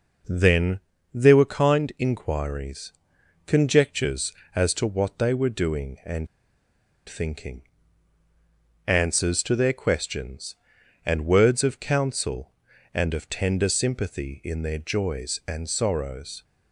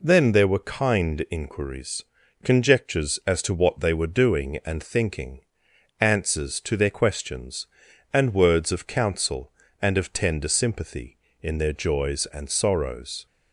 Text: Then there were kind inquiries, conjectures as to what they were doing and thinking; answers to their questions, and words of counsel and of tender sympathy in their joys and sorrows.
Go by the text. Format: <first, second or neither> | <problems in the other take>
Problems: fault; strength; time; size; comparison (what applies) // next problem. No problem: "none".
second | pauses between "Then" and "there"; slight; at 0.7 s; 0.34 s long // pauses between "and" and "thinking"; noticeable; at 6.2 s; 0.79 s long